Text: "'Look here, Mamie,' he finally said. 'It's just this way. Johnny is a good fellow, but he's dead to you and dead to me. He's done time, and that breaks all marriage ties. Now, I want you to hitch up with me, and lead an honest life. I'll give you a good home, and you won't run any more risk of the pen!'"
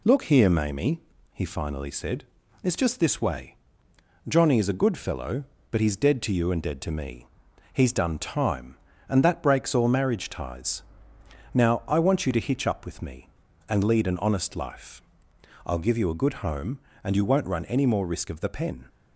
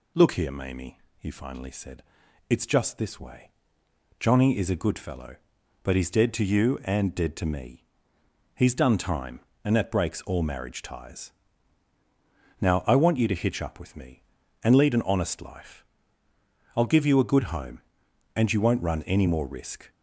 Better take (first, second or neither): first